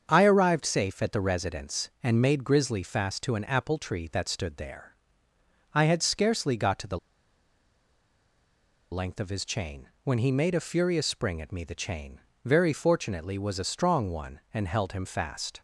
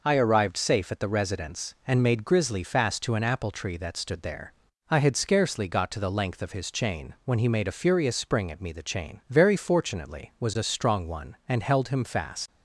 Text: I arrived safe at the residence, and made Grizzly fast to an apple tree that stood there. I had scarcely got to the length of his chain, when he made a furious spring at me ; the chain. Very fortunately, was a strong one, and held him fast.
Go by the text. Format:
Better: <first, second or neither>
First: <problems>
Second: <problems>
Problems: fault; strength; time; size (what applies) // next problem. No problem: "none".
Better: second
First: starts louder than the rest; until 1.0 s; 7 dB // pauses between "the" and "length"; strong; at 6.9 s; 1.9 s long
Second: none